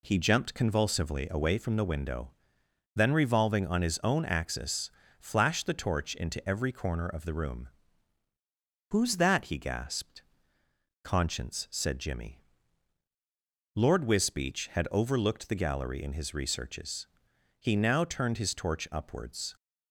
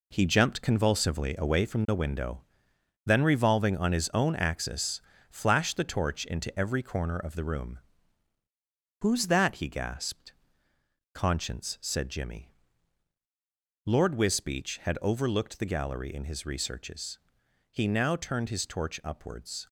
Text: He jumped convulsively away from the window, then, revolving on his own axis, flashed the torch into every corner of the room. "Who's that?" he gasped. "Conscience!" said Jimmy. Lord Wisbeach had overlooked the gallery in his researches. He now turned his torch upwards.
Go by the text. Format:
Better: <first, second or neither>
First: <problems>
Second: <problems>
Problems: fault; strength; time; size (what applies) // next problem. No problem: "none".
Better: first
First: none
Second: gets quieter; strong; throughout; 7.5 dB